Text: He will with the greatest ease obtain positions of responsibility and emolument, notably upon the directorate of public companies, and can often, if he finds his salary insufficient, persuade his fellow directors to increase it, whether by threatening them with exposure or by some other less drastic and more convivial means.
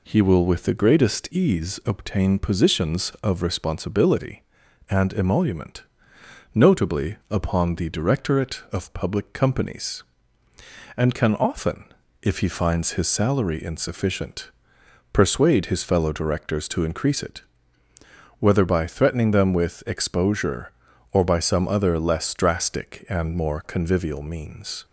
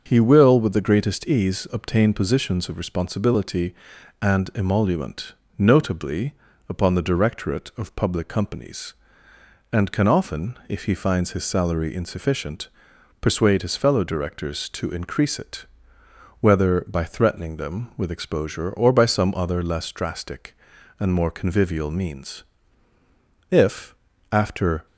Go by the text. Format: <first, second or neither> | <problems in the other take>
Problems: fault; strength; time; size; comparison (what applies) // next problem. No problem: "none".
first | starts louder than the rest; until 1.0 s; 6.5 dB // pauses between "notably" and "upon"; slight; at 6.3 s; 0.36 s long // goes on to say "If after"; from 23.4 s on; 1.3 s long